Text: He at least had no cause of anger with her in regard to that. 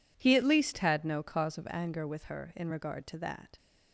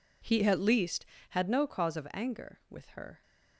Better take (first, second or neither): first